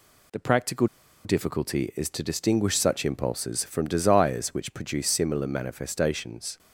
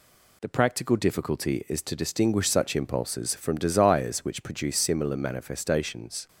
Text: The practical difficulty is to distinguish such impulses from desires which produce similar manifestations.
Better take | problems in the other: second | pauses between "practical" and "difficulty"; at 0.8 s; 0.39 s long

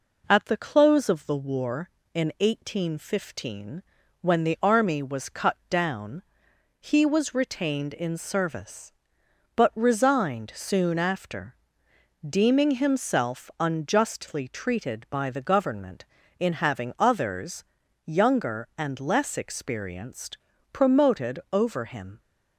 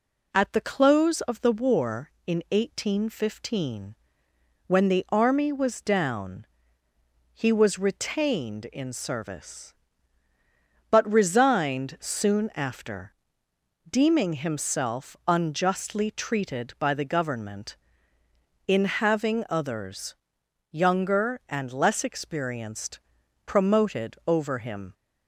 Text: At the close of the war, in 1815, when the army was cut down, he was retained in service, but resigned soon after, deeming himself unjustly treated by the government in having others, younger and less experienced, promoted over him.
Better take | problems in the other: first | skips "cut"; at 5.8 s

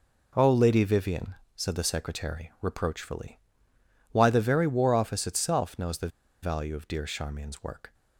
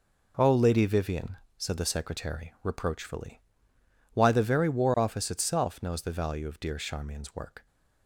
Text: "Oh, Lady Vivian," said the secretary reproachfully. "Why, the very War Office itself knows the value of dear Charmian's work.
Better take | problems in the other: second | pauses between "the" and "value"; slight; at 6.0 s; 0.34 s long

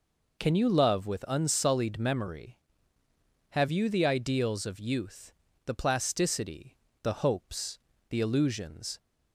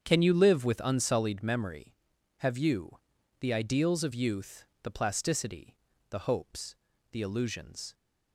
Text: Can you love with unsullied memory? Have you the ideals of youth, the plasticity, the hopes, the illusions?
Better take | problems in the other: first | starts louder than the rest; strong; until 1.0 s; 8 dB // says "live" for "love"; at 0.3 s // pauses between "you" and "the"; at 2.9 s; 0.42 s long

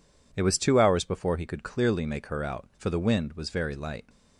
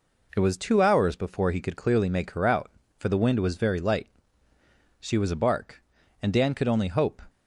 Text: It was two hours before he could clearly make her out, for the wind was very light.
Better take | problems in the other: first | goes on to say "She was a bark and Dan could only hope"; strong; from 5.0 s on; 2.2 s long

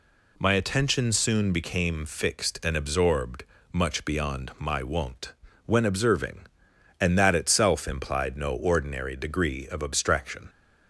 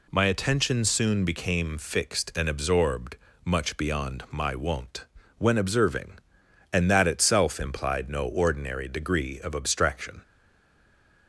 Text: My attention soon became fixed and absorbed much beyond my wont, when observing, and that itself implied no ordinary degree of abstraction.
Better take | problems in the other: first | pauses between "absorbed" and "much"; slight; at 3.1 s; 0.26 s long; slight in the first // stays silent after the last word; from 10.2 s on; 1.0 s long

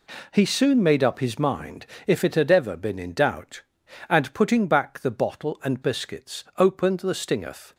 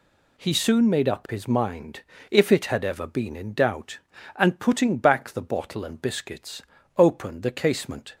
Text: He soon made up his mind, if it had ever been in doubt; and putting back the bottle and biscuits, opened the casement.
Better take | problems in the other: second | says "stingeth" for "casement"; at 7.1 s

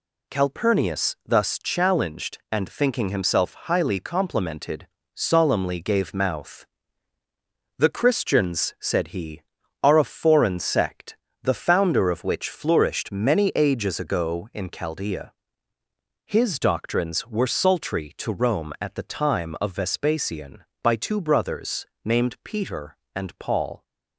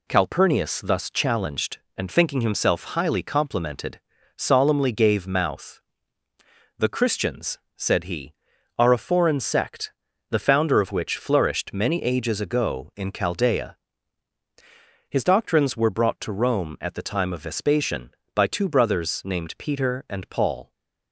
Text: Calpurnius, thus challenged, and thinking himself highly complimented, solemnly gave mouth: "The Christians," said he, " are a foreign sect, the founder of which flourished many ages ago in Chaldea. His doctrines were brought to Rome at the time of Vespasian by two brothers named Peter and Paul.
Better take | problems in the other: second | says "sultry" for "brought"; at 17.5 s // pauses between "brothers" and "named"; slight; at 21.8 s; 0.20 s long

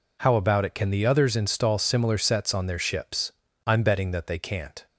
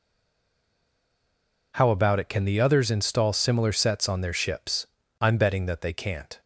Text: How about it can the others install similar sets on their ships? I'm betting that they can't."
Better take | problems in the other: first | stays silent before the first word; noticeable; until 1.7 s; 1.7 s long

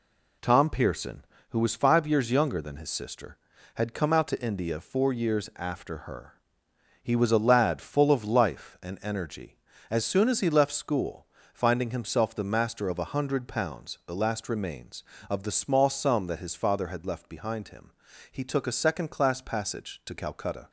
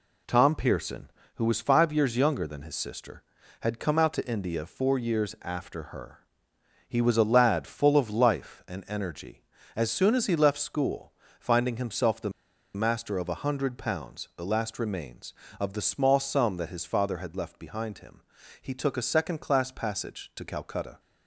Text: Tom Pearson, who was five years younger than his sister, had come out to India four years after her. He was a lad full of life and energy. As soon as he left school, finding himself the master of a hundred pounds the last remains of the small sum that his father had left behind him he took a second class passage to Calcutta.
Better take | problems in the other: first | pauses between "the" and "master"; at 12.3 s; 0.43 s long // pauses between "him" and "he"; at 18.2 s; 0.40 s long; also in the first

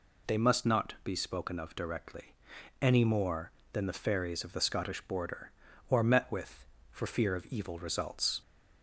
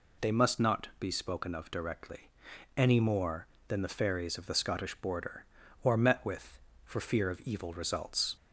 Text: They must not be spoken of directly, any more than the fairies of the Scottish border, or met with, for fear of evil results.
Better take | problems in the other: neither | none

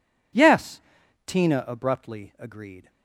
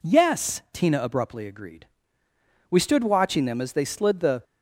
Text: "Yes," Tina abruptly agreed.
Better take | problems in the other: first | goes on to say "We stood watching them as they slid the"; strong; from 2.6 s on; 1.7 s long

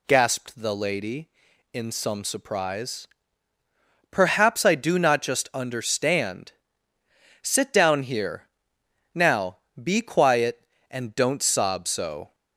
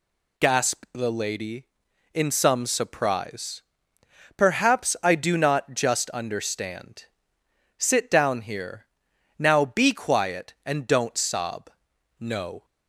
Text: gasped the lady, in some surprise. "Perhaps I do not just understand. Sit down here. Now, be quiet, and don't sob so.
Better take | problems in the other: first | says "no" for "so"; at 12.1 s

